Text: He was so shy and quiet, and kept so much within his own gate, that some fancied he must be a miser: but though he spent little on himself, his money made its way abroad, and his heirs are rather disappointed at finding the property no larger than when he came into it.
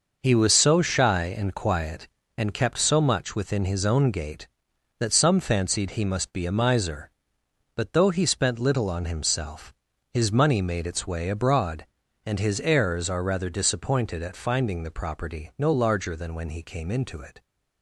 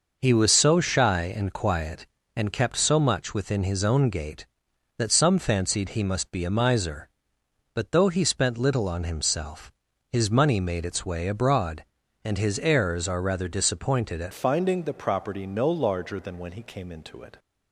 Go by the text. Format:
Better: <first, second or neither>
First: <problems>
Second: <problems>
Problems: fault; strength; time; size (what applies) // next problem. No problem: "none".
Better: first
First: none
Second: changes voice at "finding"; from 14.3 s on; 3.0 s long